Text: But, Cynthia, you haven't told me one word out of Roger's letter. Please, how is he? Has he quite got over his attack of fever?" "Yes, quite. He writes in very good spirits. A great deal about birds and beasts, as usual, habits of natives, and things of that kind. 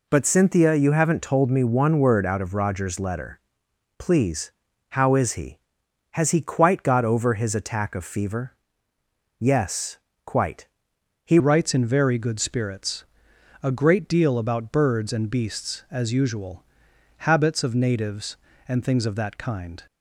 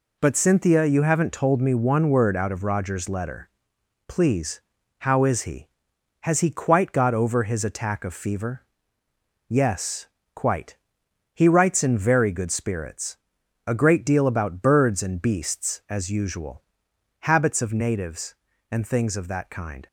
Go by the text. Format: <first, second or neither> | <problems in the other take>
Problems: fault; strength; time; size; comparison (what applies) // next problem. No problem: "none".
second | changes voice at "writes"; from 11.3 s on; 8.5 s long